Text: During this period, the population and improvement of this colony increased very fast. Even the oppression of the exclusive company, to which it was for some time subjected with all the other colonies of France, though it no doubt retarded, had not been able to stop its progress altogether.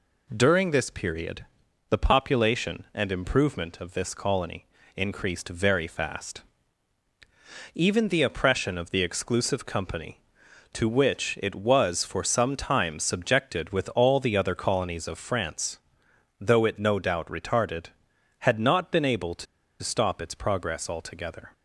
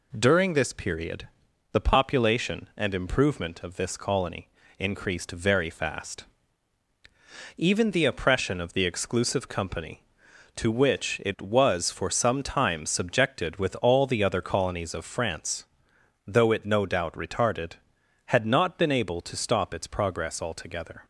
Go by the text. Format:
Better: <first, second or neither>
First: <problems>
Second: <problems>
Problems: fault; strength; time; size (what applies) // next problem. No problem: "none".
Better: second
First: pauses between "colony" and "increased"; slight; at 4.6 s; 0.28 s long // pauses between "to" and "stop"; at 19.4 s; 0.37 s long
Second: pauses between "colony" and "increased"; slight; at 4.4 s; 0.28 s long